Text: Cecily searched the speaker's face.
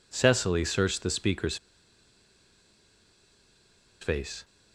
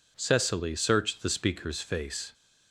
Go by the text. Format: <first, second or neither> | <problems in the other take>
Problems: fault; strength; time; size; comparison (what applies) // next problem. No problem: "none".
second | pauses between "speaker's" and "face"; strong; at 1.5 s; 2.4 s long